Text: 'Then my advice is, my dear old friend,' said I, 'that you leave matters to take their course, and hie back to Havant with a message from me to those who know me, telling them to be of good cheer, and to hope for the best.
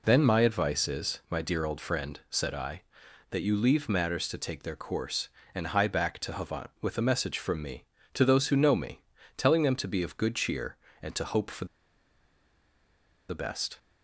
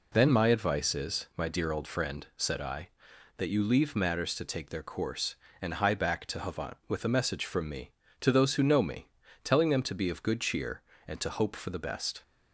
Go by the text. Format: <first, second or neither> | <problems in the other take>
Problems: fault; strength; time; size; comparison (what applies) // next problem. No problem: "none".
second | pauses between "for" and "the"; strong; at 11.6 s; 1.6 s long